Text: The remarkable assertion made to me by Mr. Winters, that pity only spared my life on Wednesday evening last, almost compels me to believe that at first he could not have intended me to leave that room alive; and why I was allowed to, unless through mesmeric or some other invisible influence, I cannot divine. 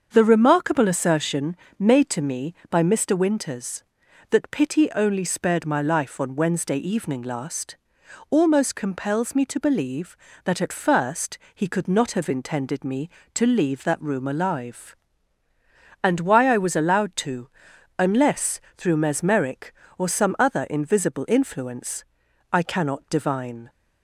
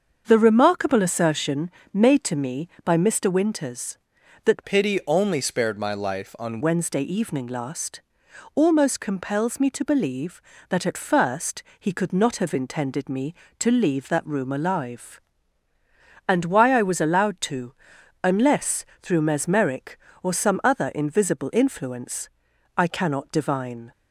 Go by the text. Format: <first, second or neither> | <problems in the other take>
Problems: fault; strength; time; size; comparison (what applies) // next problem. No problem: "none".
first | starts louder than the rest; until 1.2 s; 7 dB; also in the first // pauses between "assertion" and "made"; slight; at 1.7 s; 0.22 s long; slight in the first // changes voice from "pity" to "on"; from 4.6 to 6.5 s; 1.9 s long // pauses between "first" and "he"; slight; at 11.6 s; 0.16 s long; slight in the first // pauses between "unless" and "through"; slight; at 18.8 s; 0.16 s long; slight in the first